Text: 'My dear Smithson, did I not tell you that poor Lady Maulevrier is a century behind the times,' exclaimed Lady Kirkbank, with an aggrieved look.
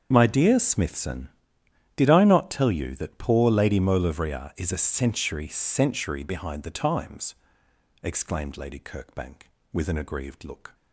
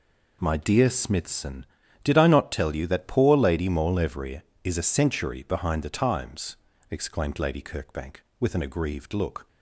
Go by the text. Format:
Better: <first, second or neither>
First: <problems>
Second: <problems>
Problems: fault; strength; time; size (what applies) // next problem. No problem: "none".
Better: second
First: starts louder than the rest; strong; until 1.1 s; 7 dB // says "century" twice; at 5.4 s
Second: none